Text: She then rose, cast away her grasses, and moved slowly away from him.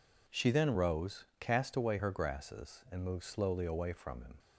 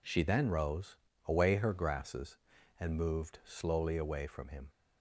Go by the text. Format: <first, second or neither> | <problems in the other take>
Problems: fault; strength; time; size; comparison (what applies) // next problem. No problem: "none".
first | skips "cast"; at 1.1 s